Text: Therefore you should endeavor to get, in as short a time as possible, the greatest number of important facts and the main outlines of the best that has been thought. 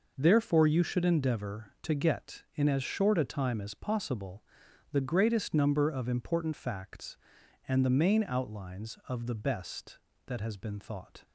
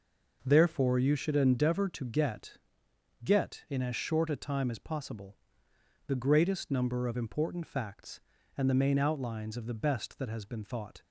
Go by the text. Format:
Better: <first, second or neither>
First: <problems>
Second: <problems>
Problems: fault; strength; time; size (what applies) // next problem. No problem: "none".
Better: first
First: none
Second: says "get" twice; at 3.2 s